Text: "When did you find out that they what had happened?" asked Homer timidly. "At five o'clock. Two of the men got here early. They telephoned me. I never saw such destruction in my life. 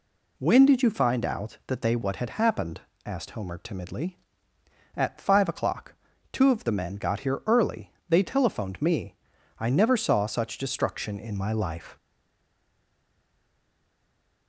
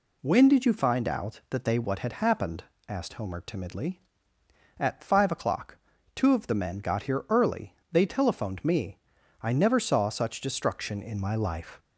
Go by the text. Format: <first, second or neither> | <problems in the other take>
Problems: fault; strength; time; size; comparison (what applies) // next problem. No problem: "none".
second | stays silent after the last word; from 11.9 s on; 2.5 s long